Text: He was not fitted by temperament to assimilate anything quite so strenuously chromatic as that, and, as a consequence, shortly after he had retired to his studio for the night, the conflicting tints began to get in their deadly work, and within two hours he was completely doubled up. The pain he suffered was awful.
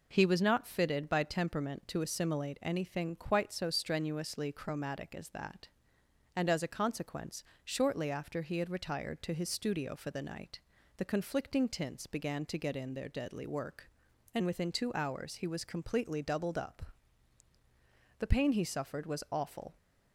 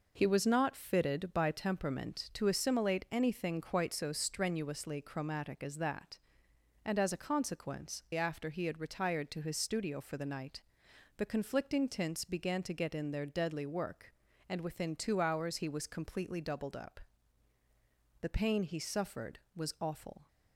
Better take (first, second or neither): first